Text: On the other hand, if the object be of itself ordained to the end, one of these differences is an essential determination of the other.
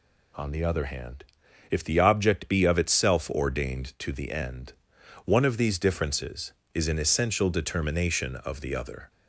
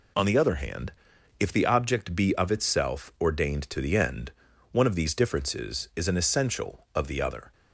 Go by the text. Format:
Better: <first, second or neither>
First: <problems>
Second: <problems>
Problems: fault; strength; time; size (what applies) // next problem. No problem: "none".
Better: first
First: none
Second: skips "determination"; at 6.8 s